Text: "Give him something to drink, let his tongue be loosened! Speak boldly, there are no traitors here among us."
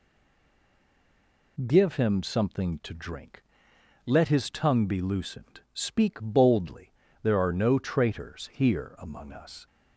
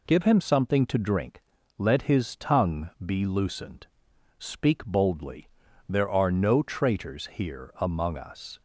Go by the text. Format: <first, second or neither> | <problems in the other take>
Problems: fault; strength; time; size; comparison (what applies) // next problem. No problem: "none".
second | stays silent before the first word; noticeable; until 1.5 s; 1.5 s long